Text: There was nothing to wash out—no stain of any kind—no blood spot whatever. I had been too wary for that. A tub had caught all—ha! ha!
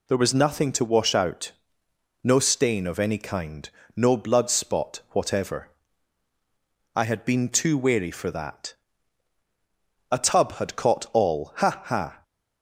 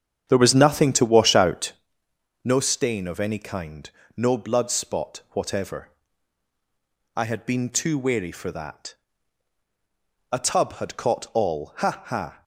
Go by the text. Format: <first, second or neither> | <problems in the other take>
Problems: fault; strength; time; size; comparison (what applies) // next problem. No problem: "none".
first | starts louder than the rest; strong; until 1.9 s; 8.5 dB